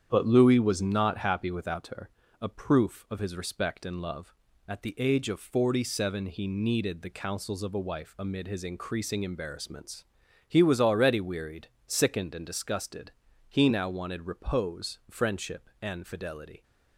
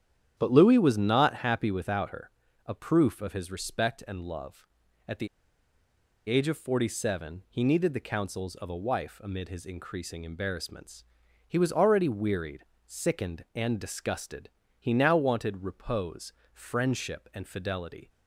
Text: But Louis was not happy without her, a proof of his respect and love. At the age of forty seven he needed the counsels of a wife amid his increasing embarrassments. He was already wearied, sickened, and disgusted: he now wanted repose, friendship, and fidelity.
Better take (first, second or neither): first